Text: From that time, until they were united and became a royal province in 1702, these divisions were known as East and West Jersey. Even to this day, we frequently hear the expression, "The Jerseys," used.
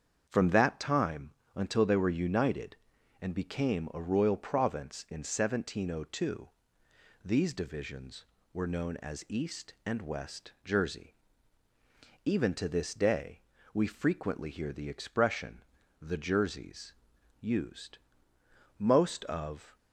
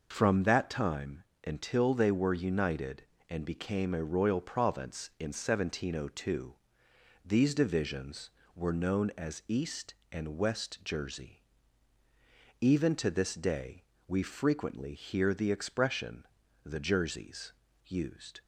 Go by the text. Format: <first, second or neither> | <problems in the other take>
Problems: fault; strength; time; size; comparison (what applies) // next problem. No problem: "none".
second | starts louder than the rest; strong; until 1.3 s; 7.5 dB // goes on to say "Most of"; noticeable; from 18.7 s on; 1.0 s long